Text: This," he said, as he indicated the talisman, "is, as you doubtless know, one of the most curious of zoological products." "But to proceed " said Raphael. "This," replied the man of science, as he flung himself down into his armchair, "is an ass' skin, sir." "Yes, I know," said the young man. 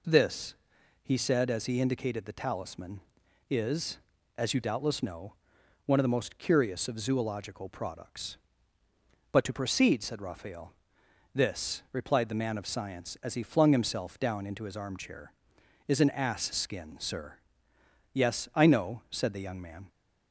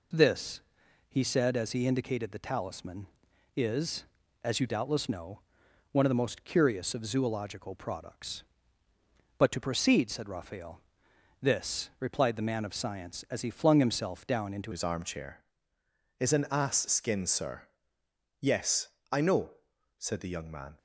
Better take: first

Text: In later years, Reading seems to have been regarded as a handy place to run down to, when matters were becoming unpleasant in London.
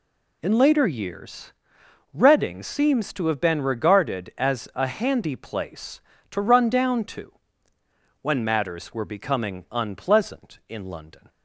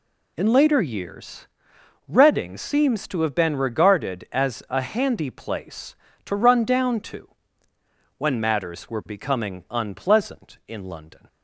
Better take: neither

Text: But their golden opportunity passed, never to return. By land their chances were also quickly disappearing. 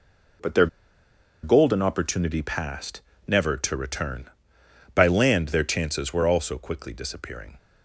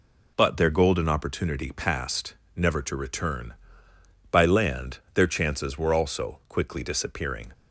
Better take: second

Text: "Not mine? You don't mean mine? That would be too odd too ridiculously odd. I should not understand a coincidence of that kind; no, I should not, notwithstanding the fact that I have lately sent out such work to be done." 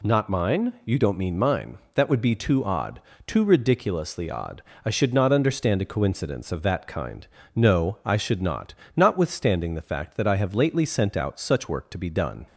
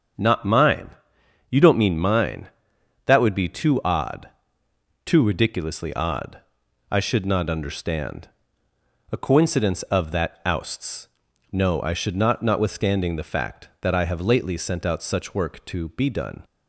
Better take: first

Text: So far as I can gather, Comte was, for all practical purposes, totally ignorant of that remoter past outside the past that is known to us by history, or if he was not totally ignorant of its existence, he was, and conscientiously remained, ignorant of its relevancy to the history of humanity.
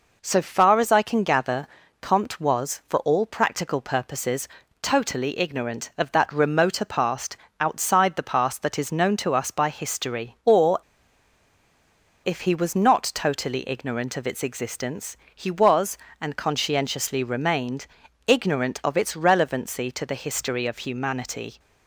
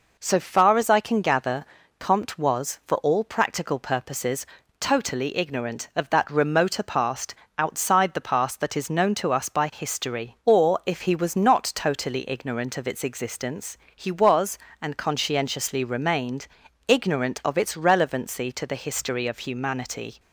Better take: second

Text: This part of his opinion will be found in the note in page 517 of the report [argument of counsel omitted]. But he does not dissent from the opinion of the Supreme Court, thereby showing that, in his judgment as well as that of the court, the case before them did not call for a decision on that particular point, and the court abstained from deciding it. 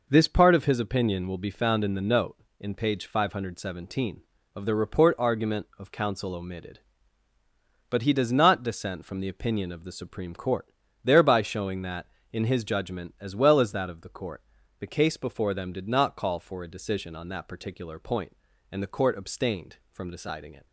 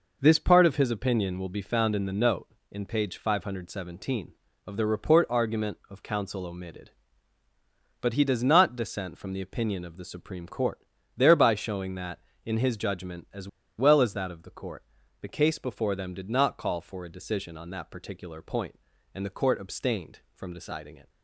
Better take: first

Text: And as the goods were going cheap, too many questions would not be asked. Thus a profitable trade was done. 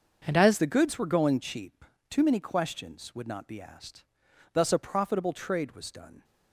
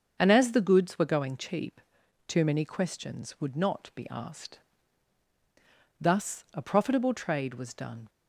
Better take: second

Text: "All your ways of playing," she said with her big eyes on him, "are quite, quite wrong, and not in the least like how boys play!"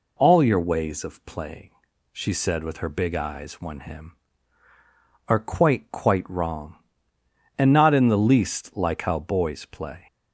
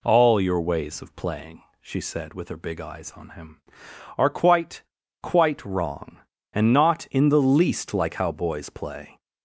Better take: second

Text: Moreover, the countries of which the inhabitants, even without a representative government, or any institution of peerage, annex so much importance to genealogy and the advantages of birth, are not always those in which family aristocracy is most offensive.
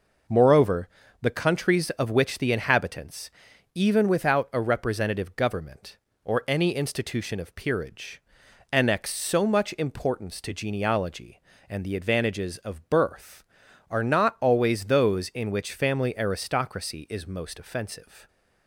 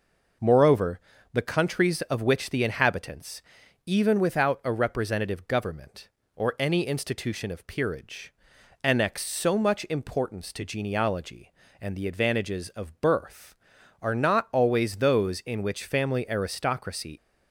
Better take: first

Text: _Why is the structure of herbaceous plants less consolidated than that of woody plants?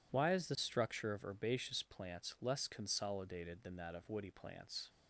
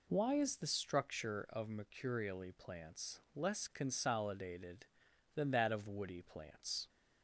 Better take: first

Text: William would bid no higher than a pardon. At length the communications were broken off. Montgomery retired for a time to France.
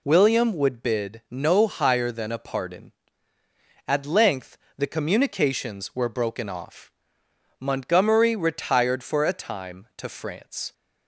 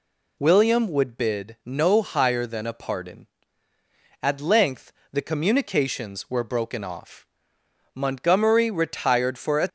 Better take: first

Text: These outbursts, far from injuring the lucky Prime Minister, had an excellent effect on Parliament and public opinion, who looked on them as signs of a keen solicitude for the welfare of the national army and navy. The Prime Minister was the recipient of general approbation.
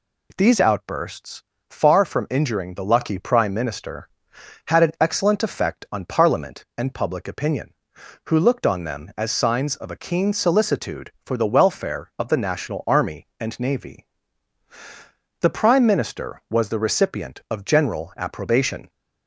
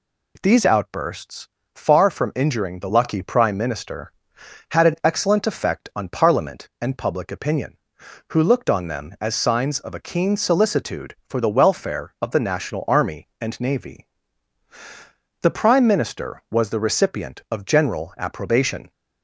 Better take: neither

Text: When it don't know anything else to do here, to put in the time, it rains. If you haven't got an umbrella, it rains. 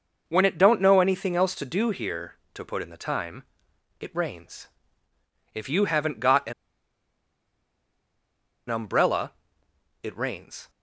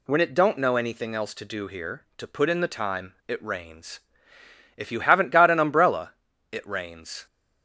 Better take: second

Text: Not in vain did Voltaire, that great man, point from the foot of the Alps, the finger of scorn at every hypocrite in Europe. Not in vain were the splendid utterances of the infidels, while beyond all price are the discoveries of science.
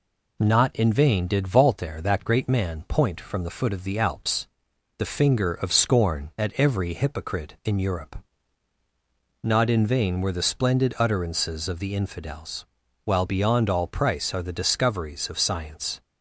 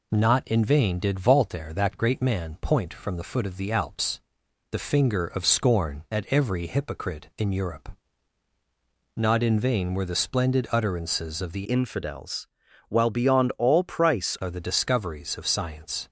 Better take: first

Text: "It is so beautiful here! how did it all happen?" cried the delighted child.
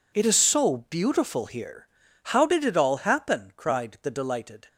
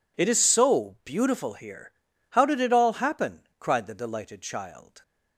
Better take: second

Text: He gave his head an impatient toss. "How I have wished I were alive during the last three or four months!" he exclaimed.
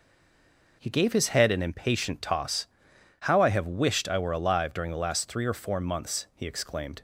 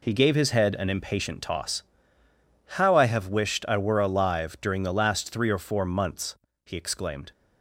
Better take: second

